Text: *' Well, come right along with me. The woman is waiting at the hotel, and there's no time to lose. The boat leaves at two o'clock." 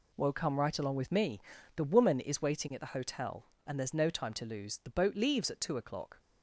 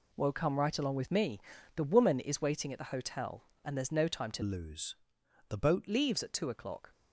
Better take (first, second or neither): first